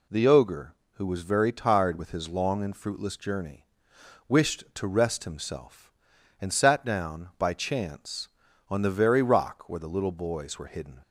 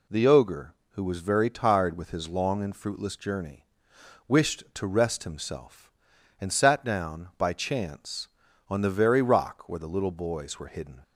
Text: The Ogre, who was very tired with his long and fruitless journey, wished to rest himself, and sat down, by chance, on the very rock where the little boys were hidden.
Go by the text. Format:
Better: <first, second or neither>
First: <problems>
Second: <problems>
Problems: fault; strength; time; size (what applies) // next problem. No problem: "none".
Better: neither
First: none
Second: none